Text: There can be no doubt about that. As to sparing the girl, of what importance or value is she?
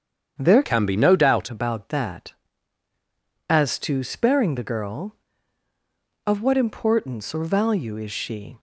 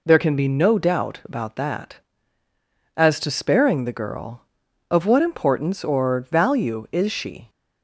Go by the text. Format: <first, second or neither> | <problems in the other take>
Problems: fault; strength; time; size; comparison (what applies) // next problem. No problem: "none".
second | starts louder than the rest; strong; until 1.4 s; 8 dB // changes voice from "can" to "doubt"; from 0.6 to 1.4 s; 0.8 s long